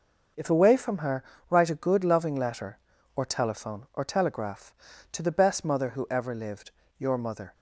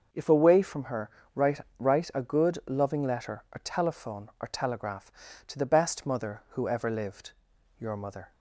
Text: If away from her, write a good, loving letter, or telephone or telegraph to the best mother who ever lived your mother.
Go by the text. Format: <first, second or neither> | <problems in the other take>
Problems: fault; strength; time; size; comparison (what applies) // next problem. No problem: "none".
first | starts louder than the rest; until 1.3 s; 6 dB // says "write" twice; at 1.7 s // pauses between "lived" and "your"; noticeable; at 7.3 s; 0.48 s long; slight in the first